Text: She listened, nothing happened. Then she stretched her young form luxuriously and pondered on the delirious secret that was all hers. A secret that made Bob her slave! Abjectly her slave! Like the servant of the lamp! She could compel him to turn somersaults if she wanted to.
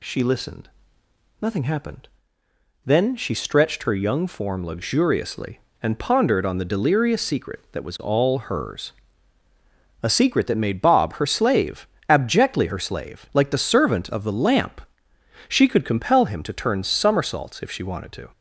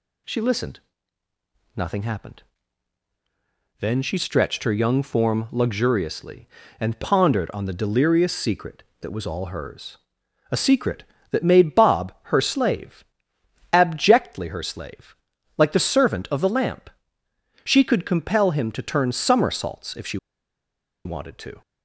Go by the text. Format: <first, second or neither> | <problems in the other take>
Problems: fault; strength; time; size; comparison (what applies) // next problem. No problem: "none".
first | pauses between "she" and "wanted"; noticeable; at 20.1 s; 0.88 s long